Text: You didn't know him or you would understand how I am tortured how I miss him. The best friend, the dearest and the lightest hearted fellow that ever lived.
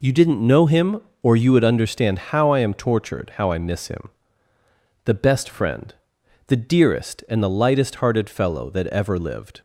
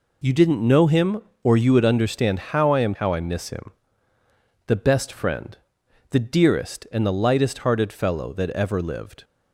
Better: first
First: none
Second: skips "tortured"; at 2.9 s

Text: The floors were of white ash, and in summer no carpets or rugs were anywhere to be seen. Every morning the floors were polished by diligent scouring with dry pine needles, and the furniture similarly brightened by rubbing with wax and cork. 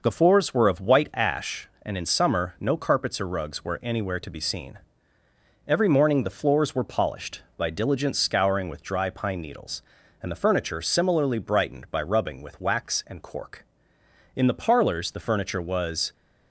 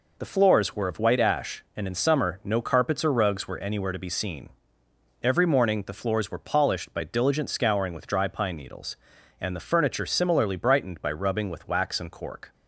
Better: second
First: goes on to say "In the parlors the furniture was"; strong; from 14.3 s on; 1.7 s long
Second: none

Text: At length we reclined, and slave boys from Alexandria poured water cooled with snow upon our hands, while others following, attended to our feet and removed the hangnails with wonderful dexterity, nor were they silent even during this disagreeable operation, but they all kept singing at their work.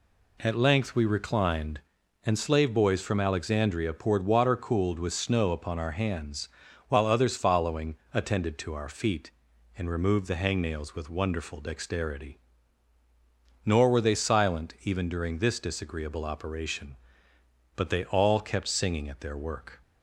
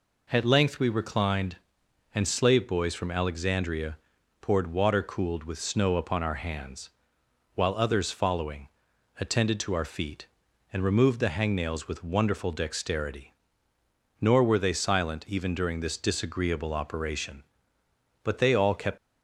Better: first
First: none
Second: pauses between "Alexandria" and "poured"; at 3.9 s; 0.44 s long // stops before "singing at their work"; at 18.9 s

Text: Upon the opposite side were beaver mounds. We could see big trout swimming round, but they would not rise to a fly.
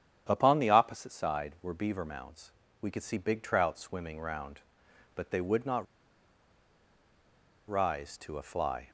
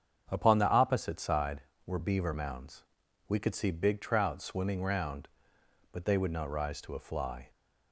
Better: second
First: starts louder than the rest; strong; until 1.3 s; 9.5 dB // pauses between "not" and "rise"; strong; at 5.8 s; 1.8 s long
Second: starts louder than the rest; strong; until 1.3 s; 7.5 dB

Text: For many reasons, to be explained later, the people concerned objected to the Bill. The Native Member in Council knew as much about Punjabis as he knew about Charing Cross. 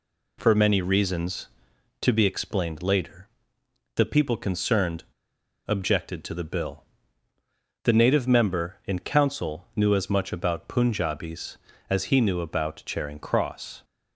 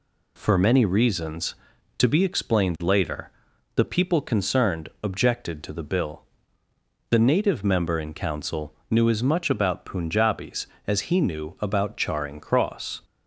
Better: second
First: pauses between "concerned" and "objected"; noticeable; at 5.0 s; 0.62 s long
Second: none

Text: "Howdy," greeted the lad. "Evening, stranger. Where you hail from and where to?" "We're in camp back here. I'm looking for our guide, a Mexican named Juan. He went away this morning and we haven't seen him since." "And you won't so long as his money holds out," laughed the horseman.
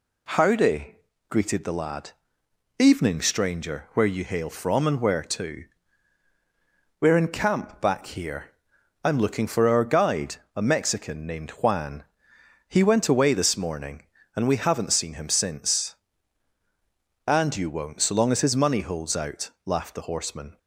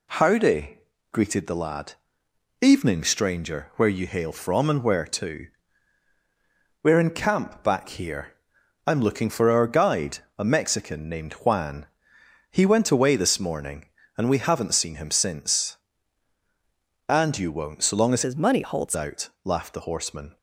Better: first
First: none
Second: changes voice from "his" to "holds"; from 18.2 to 18.9 s; 0.7 s long

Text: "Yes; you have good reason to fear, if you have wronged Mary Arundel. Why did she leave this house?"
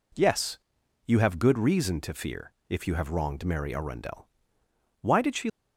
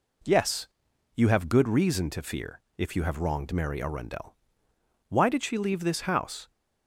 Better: second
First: stops before "leave this house"; at 5.4 s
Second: none

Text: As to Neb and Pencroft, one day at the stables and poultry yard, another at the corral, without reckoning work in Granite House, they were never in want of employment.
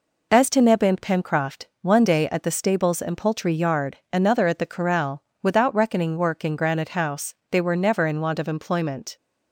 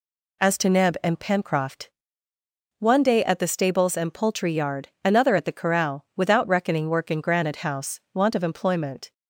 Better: first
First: none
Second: skips "they were never in"; at 8.0 s

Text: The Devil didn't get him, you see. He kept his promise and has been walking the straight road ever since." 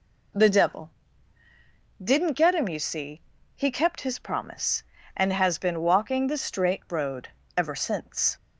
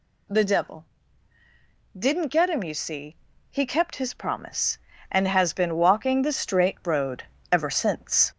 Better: first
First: pauses between "Devil" and "didn't"; at 0.8 s; 1.1 s long // pauses between "road" and "ever"; slight; at 7.2 s; 0.28 s long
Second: gets louder; noticeable; throughout; 4 dB // pauses between "Devil" and "didn't"; at 0.8 s; 1.1 s long // pauses between "road" and "ever"; slight; at 7.2 s; 0.28 s long

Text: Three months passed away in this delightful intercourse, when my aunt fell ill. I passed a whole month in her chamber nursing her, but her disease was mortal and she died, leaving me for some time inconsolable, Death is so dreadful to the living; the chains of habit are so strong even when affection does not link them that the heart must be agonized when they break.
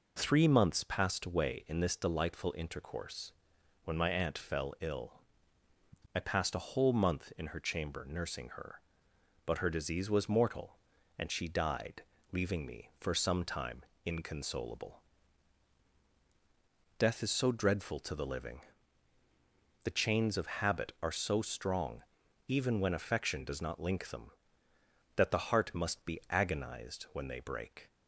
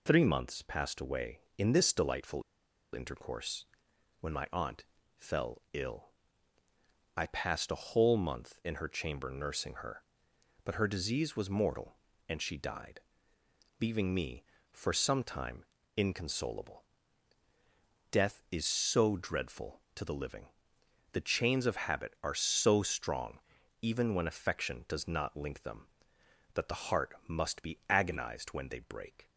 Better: first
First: pauses between "time" and "inconsolable"; slight; at 13.8 s; 0.22 s long // pauses between "strong" and "even"; noticeable; at 22.0 s; 0.46 s long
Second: pauses between "delightful" and "intercourse"; noticeable; at 2.4 s; 0.52 s long // pauses between "aunt" and "fell"; slight; at 4.8 s; 0.30 s long // pauses between "time" and "inconsolable"; slight; at 15.6 s; 0.32 s long // pauses between "strong" and "even"; at 23.4 s; 0.42 s long

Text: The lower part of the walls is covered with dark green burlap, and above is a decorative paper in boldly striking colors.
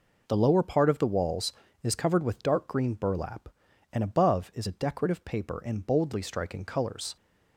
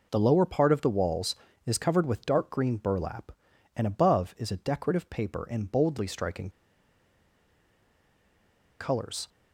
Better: first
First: none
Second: pauses between "striking" and "colors"; strong; at 6.4 s; 2.3 s long

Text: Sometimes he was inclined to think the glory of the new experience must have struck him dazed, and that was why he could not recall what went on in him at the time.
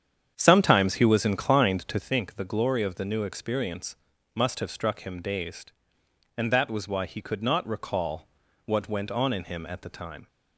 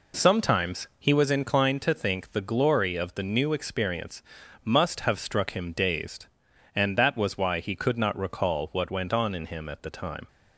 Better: second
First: starts louder than the rest; strong; until 2.2 s; 8.5 dB // pauses between "experience" and "must"; at 3.9 s; 0.38 s long // pauses between "recall" and "what"; slight; at 8.2 s; 0.36 s long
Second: pauses between "experience" and "must"; at 4.2 s; 0.40 s long

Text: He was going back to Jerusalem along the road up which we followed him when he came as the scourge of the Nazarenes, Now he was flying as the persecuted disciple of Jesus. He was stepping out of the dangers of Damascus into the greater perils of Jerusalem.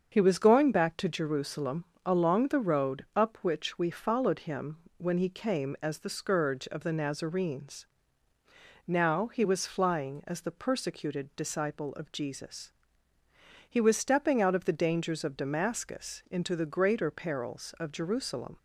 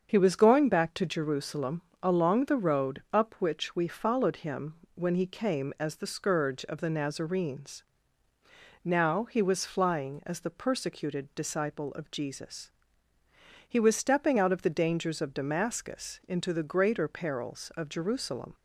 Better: neither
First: starts louder than the rest; until 1.1 s; 7 dB // pauses between "Jerusalem" and "along"; slight; at 1.8 s; 0.20 s long // pauses between "him" and "when"; slight; at 4.7 s; 0.22 s long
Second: starts louder than the rest; until 1.1 s; 7 dB // pauses between "Jerusalem" and "along"; slight; at 1.8 s; 0.20 s long // pauses between "him" and "when"; slight; at 4.7 s; 0.22 s long

